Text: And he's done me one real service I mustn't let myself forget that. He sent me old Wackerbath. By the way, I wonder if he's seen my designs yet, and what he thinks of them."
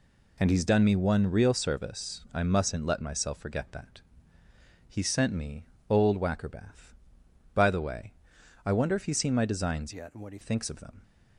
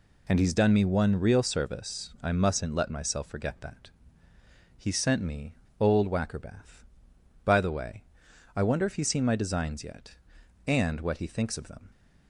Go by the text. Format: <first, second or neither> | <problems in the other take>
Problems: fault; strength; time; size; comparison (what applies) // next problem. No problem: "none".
second | pauses between "me" and "old"; slight; at 5.6 s; 0.24 s long; slight in the second // changes voice from "yet" to "he"; from 9.9 to 10.3 s; 0.4 s long